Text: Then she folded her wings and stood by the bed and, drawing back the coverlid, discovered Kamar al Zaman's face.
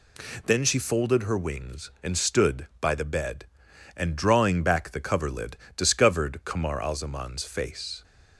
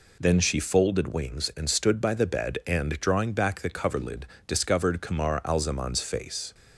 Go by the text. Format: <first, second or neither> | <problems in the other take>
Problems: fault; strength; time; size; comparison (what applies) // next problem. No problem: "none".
first | skips "her"; at 1.1 s